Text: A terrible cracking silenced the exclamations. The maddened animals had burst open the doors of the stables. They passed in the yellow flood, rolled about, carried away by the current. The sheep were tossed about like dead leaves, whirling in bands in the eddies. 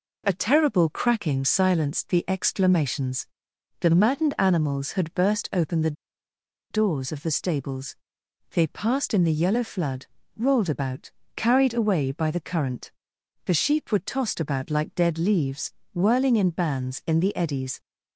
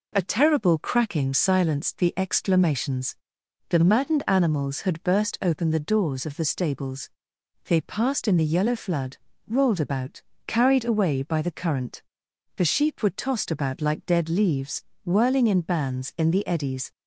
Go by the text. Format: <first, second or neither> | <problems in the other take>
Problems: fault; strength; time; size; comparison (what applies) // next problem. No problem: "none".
second | pauses between "the" and "doors"; noticeable; at 5.9 s; 0.77 s long